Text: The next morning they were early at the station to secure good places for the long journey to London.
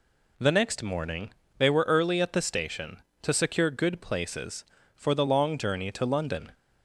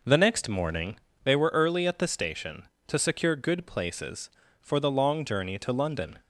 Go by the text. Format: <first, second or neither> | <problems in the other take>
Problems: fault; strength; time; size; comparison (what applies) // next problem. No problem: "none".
first | starts louder than the rest; noticeable; until 1.0 s; 5.5 dB // pauses between "morning" and "they"; slight; at 0.9 s; 0.30 s long; slight in the first